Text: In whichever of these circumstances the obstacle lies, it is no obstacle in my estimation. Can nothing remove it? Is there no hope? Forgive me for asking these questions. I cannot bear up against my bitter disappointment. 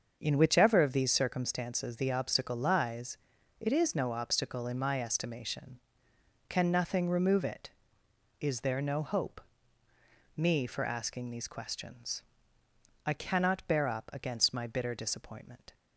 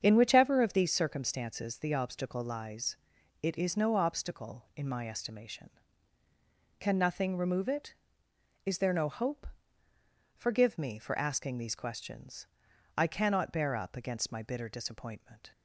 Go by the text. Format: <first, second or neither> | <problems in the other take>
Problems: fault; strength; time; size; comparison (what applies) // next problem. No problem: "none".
second | starts louder than the rest; until 1.2 s; 6.5 dB; strong in the second // skips "Forgive"; at 9.9 s